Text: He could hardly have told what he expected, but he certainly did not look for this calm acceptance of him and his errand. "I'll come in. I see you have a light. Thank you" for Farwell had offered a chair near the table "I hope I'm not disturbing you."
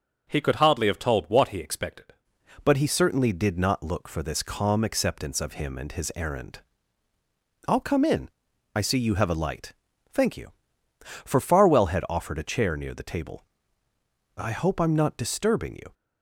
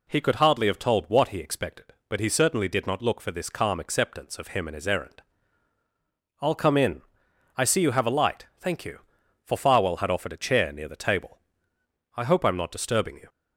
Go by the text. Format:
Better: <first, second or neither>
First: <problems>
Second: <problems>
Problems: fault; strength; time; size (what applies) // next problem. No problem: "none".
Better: second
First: starts louder than the rest; until 1.3 s; 6.5 dB // changes voice at "but"; from 2.6 s on; 13.3 s long // pauses between "table" and "I"; noticeable; at 13.4 s; 0.90 s long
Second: pauses between "table" and "I"; noticeable; at 11.3 s; 0.76 s long